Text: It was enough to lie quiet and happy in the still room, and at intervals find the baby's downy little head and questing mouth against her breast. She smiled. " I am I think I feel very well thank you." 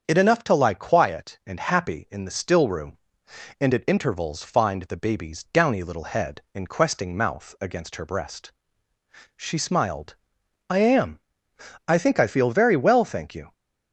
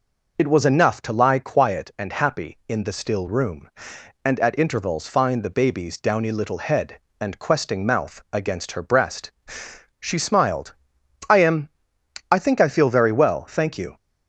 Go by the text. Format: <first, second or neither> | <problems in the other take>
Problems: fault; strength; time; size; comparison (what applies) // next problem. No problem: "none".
second | starts louder than the rest; until 1.0 s; 7 dB // skips "was"; at 0.1 s // pauses between "am" and "I"; noticeable; at 11.2 s; 0.68 s long; noticeable in the second